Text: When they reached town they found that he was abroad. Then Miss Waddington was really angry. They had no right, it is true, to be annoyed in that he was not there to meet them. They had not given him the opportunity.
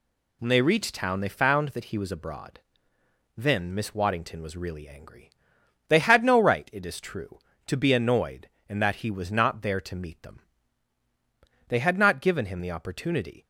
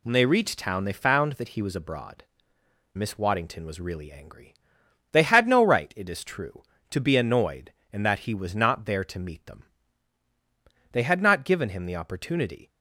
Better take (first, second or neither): first